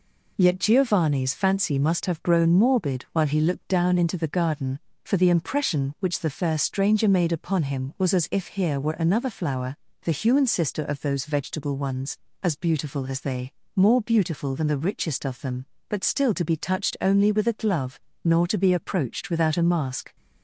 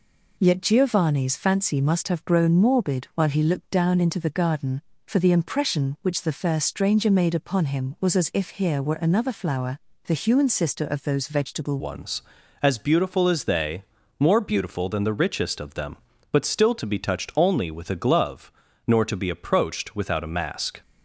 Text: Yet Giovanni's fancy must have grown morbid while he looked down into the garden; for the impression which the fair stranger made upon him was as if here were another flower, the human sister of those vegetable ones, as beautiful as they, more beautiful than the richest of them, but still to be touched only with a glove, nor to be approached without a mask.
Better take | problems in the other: first | changes voice at "ones"; from 11.7 s on; 9.1 s long

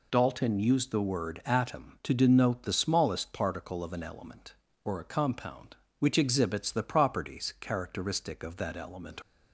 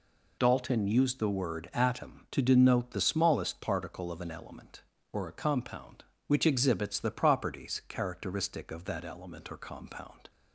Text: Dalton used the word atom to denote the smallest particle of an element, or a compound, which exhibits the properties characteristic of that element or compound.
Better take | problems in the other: second | stops before "or compound"; at 9.2 s

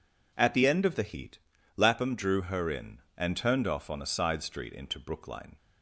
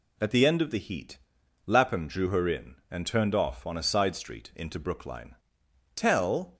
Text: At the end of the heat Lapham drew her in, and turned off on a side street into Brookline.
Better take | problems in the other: first | pauses between "heat" and "Lapham"; noticeable; at 1.1 s; 0.48 s long; slight in the first // goes on to say "Tell"; noticeable; from 5.9 s on; 0.62 s long

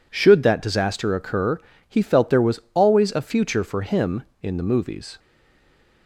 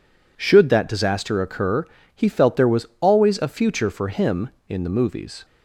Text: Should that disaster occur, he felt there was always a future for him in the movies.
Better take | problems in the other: second | stays silent after the last word; slight; from 5.1 s on; 0.9 s long

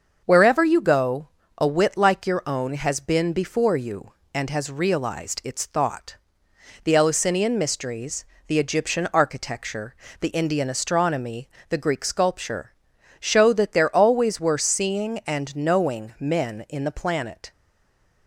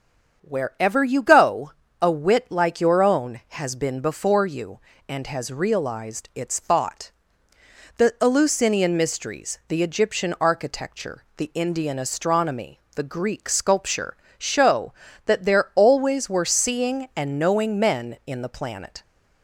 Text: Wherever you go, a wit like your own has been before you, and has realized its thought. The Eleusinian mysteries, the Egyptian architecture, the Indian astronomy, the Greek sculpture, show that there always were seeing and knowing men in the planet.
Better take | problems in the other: second | starts louder than the rest; until 1.2 s; 6.5 dB; strong in the second // stays silent after the last word; slight; from 17.5 s on; 0.7 s long

